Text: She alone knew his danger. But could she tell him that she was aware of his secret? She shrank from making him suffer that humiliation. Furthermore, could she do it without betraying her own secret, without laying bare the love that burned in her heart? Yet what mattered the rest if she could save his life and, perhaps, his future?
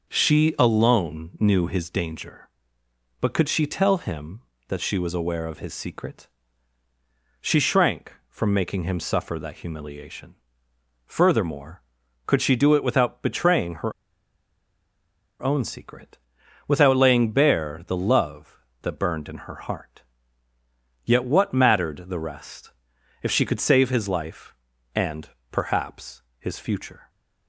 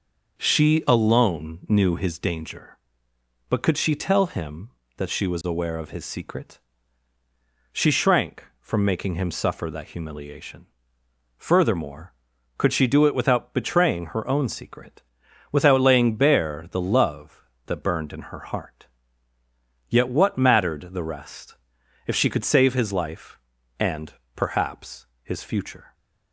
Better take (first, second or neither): second